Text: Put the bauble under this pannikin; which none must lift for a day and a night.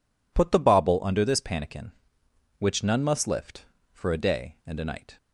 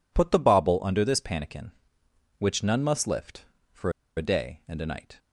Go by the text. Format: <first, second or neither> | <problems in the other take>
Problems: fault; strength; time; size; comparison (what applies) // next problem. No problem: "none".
first | pauses between "for" and "a"; slight; at 3.9 s; 0.25 s long